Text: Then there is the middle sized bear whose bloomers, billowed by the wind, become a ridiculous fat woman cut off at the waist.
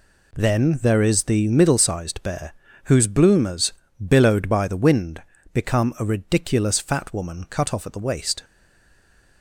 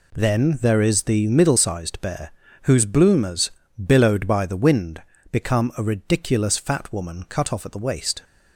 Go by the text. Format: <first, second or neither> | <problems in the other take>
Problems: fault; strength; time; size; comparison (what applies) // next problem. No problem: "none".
second | pauses between "bear" and "whose"; slight; at 2.5 s; 0.32 s long; slight in the second // stays silent after the last word; from 8.4 s on; 1.0 s long